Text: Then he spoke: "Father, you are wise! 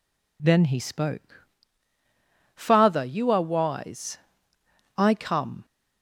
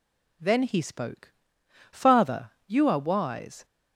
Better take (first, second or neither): second